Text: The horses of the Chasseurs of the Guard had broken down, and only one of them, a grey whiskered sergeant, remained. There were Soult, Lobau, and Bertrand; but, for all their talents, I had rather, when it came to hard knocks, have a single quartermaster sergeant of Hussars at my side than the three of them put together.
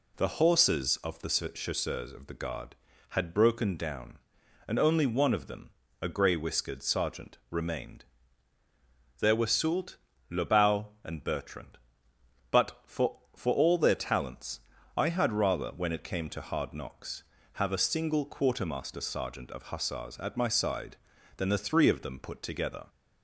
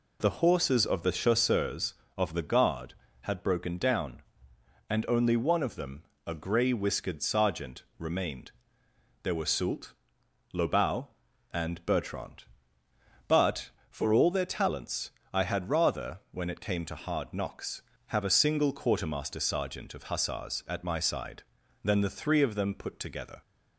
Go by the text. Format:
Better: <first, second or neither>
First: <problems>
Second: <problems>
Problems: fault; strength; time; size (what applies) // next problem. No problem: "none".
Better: second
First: says "for" twice; at 13.3 s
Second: none